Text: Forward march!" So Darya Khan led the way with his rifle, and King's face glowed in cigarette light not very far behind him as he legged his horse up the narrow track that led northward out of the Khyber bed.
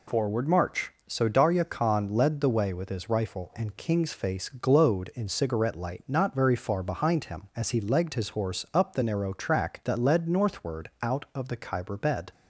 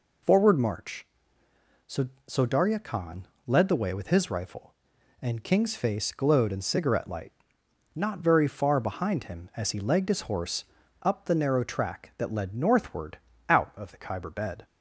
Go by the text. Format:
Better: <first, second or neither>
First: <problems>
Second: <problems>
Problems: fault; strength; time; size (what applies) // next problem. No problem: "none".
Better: first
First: none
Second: says "So" twice; at 2.2 s // pauses between "Khan" and "led"; slight; at 3.2 s; 0.20 s long // pauses between "light" and "not"; noticeable; at 7.3 s; 0.60 s long // pauses between "horse" and "up"; at 10.6 s; 0.40 s long // pauses between "northward" and "out"; slight; at 13.1 s; 0.32 s long